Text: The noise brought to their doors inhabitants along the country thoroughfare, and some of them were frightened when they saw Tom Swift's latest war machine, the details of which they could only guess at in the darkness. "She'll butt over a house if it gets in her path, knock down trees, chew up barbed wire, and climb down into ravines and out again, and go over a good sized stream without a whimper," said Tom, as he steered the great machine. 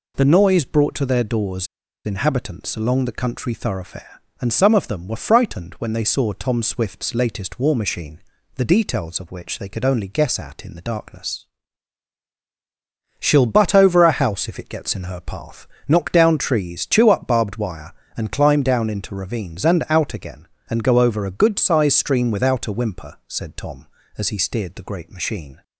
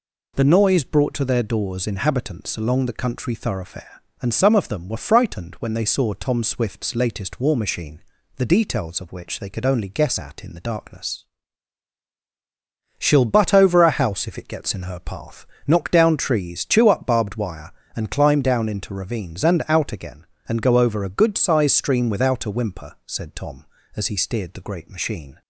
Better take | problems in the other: second | pauses between "doors" and "inhabitants"; at 1.6 s; 0.38 s long

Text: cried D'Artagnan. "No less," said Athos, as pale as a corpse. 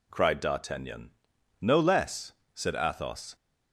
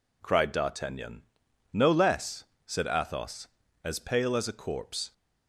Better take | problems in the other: second | stops before "as pale as a corpse"; at 3.3 s

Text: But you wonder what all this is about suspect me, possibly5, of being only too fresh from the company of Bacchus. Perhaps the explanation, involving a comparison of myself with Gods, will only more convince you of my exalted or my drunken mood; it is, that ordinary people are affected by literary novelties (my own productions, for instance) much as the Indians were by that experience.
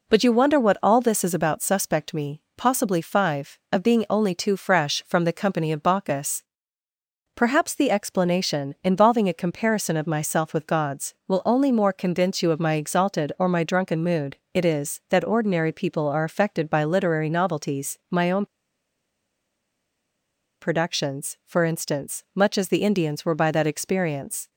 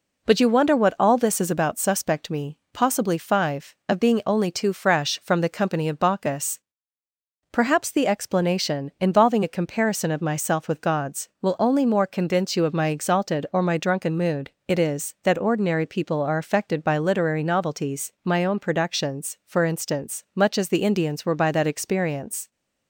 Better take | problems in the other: second | pauses between "own" and "productions"; strong; at 18.4 s; 2.1 s long

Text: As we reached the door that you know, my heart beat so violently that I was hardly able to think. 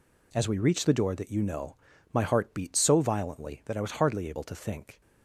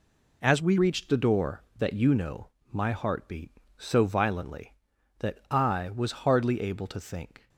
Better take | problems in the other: first | changes voice at "reached"; from 0.7 s on; 6.7 s long

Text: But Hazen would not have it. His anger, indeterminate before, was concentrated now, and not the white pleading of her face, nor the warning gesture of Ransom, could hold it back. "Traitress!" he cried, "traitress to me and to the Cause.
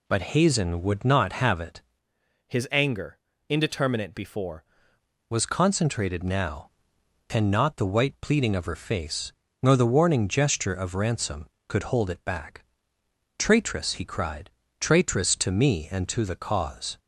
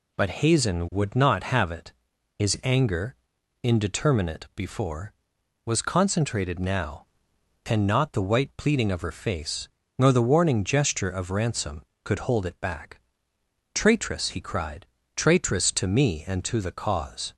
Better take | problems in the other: second | changes voice from "His" to "before"; from 2.4 to 4.6 s; 2.2 s long

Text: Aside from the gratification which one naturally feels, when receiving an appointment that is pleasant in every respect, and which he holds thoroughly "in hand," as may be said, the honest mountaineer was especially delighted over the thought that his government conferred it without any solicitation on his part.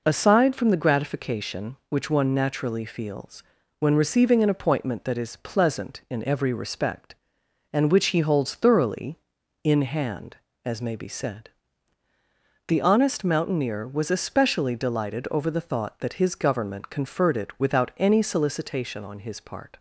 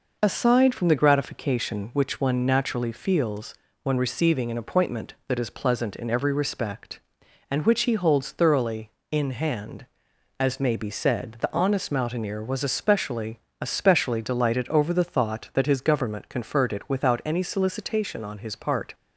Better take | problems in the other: first | says "especially" twice; at 13.6 s

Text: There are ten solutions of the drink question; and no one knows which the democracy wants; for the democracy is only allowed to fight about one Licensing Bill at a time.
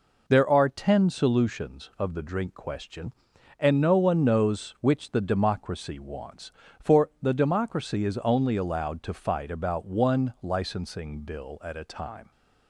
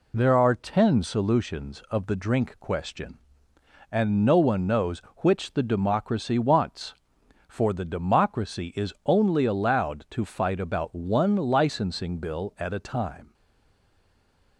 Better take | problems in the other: first | stays silent after the last word; noticeable; from 13.3 s on; 1.2 s long

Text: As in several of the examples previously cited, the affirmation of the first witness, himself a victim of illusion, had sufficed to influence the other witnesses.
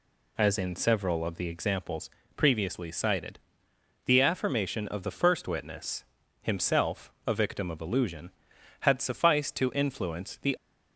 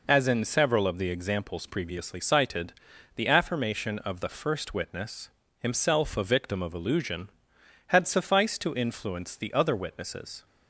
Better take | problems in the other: second | pauses between "examples" and "previously"; slight; at 2.0 s; 0.26 s long // stops before "other witnesses"; at 10.5 s

